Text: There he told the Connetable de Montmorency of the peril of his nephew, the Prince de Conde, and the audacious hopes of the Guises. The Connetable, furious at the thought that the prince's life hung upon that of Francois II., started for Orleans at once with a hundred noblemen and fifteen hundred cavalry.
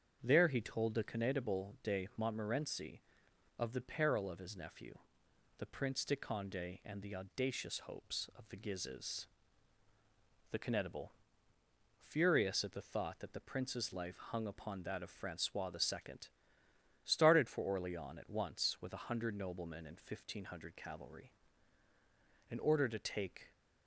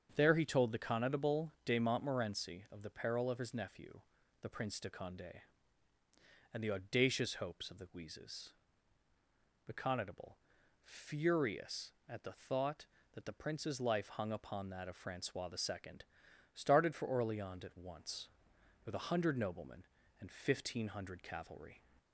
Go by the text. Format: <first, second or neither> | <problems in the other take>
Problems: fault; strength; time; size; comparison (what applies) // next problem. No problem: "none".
second | starts louder than the rest; strong; until 1.2 s; 7 dB; also in the second // goes on to say "In order to take"; noticeable; from 22.4 s on; 1.0 s long